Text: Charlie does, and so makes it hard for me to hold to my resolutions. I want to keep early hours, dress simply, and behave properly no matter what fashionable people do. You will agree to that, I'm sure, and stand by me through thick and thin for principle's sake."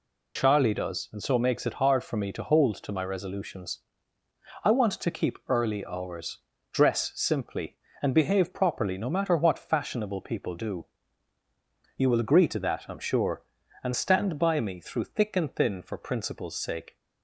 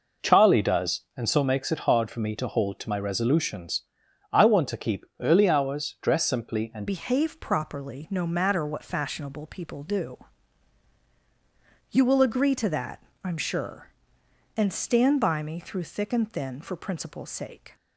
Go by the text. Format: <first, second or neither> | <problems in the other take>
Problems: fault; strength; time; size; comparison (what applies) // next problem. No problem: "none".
first | changes voice at "behave"; from 6.8 s on; 10.9 s long